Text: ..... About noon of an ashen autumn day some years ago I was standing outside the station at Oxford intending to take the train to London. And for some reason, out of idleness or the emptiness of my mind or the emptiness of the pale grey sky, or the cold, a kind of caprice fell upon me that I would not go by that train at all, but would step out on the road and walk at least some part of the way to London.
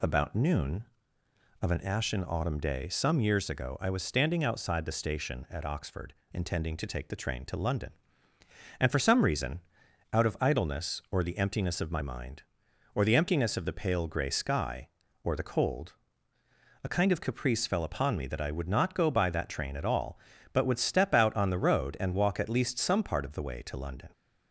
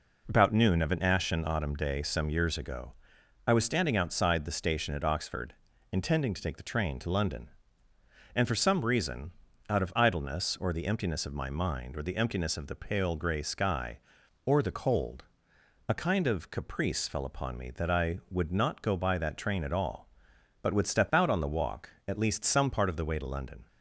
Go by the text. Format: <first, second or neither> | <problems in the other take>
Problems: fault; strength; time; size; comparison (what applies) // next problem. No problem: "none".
first | pauses between "ago" and "I"; noticeable; at 2.9 s; 0.52 s long // pauses between "Oxford" and "intending"; at 5.5 s; 0.38 s long; slight in the first // skips "road and"; at 21.4 s